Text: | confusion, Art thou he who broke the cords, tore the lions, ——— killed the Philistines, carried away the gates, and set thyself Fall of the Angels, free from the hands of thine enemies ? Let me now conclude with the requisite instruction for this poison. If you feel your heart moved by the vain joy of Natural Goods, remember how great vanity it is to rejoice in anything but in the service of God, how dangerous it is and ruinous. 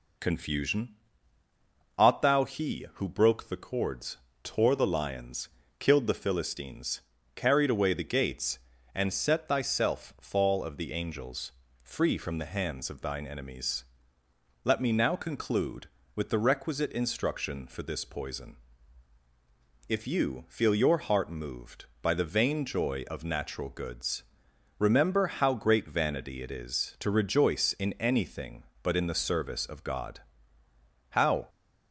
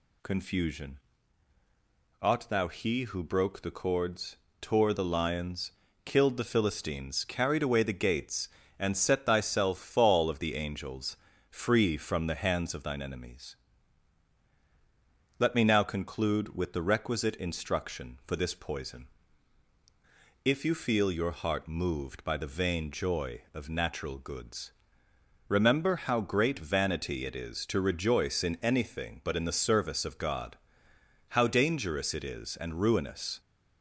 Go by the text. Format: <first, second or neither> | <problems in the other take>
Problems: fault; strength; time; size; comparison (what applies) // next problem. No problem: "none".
second | stops before "dangerous it is and ruinous"; at 31.4 s